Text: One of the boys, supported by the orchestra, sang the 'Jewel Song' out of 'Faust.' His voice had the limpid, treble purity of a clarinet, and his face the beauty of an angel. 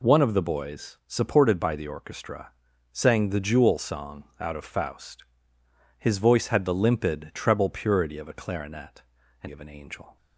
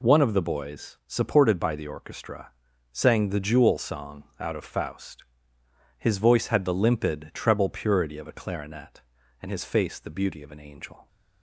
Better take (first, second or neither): second